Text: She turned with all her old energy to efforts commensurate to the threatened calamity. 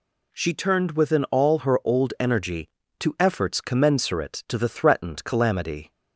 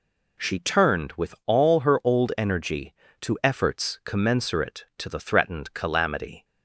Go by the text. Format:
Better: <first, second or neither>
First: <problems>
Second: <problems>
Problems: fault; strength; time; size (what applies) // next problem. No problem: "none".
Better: second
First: says "within" for "with"; at 0.9 s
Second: none